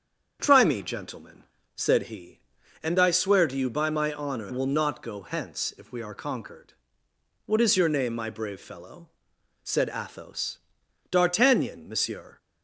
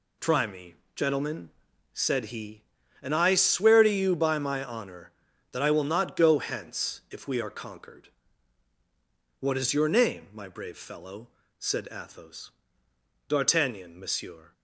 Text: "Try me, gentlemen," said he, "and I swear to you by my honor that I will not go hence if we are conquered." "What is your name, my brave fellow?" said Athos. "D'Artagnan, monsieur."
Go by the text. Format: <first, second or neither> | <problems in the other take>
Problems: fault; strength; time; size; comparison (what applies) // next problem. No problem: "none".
second | starts louder than the rest; strong; until 1.4 s; 7.5 dB // skips "that I"; at 4.5 s